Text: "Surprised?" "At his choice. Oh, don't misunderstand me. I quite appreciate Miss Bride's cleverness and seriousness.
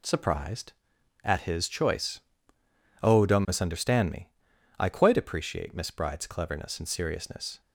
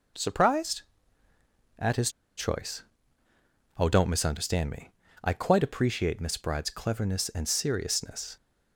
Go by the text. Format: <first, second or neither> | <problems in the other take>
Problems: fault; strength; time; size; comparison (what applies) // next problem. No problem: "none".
first | pauses between "his" and "choice"; slight; at 2.1 s; 0.26 s long